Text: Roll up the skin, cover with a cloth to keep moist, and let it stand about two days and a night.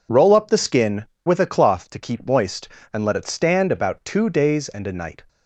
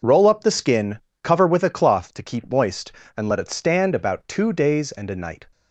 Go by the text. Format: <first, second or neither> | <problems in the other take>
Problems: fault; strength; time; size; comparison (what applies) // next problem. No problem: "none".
second | skips "cover"; at 1.1 s